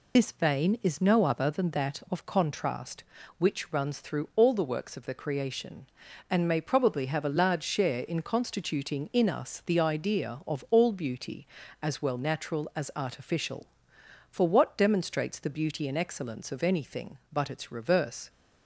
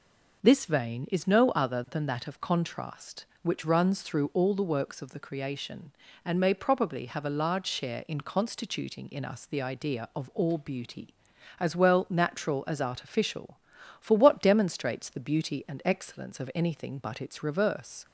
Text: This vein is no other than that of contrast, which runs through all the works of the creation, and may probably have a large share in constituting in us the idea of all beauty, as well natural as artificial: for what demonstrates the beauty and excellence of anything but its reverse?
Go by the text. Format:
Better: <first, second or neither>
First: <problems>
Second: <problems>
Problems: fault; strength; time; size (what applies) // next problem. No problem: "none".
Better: second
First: loses the start of "This"; at 0.1 s; 55 ms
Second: none